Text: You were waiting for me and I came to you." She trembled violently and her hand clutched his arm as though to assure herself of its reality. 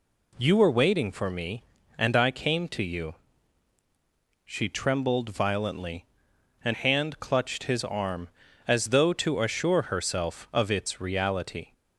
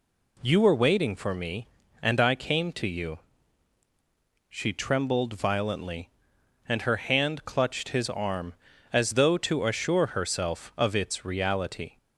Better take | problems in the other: second | skips "her"; at 6.7 s

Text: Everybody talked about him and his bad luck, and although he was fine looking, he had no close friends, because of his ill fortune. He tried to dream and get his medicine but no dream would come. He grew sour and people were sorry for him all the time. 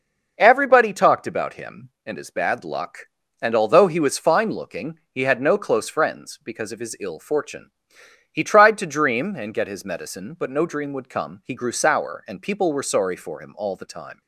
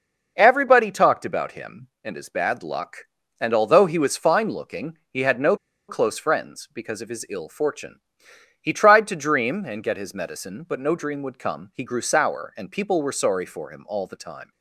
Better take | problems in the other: first | pauses between "no" and "close"; slight; at 5.5 s; 0.32 s long

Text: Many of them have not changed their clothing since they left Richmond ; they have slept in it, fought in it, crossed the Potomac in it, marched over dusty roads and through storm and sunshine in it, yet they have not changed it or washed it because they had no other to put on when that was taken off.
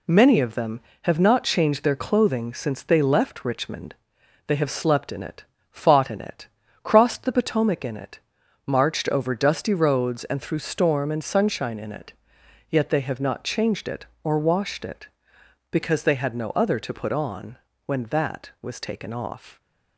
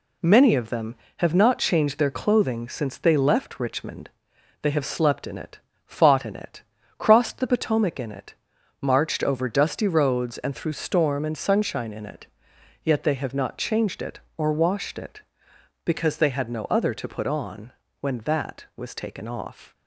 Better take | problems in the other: neither | pauses between "on" and "when"; slight; the same in both

